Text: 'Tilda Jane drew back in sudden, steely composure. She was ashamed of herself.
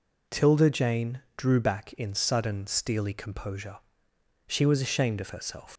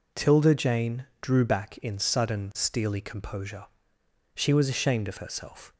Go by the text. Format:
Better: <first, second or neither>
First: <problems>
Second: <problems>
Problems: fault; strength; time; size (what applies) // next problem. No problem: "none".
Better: second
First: pauses between "Jane" and "drew"; slight; at 1.2 s; 0.16 s long // leaves "herself" unfinished; at 5.7 s; 100 ms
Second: pauses between "Jane" and "drew"; slight; at 1.0 s; 0.16 s long